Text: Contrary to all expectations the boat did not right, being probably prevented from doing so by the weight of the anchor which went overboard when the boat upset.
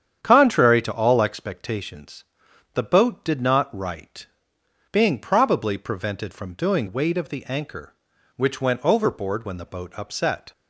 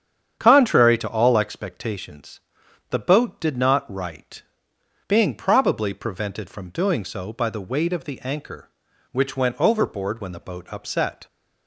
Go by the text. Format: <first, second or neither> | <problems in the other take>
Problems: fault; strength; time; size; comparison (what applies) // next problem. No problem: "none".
second | starts louder than the rest; strong; until 1.2 s; 8.5 dB; strong in the second // pauses between "expectations" and "the"; noticeable; at 2.2 s; 0.50 s long; noticeable in the second // skips "so by the"; at 6.8 s